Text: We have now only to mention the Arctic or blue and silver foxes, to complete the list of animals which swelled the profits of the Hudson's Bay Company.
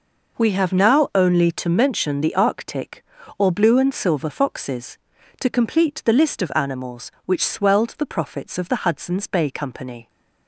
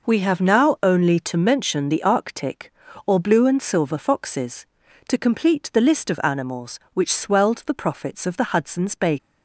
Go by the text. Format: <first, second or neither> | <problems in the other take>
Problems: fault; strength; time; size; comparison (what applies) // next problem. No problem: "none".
first | stops before "Company"; at 9.1 s